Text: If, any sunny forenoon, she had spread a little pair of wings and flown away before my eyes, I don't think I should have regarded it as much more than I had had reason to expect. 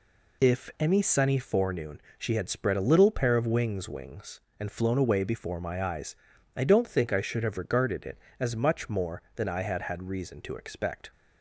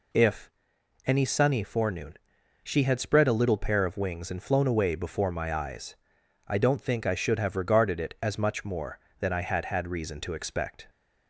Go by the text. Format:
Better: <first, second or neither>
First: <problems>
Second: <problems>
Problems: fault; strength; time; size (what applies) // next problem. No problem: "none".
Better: second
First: says "wings" twice; at 3.8 s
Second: none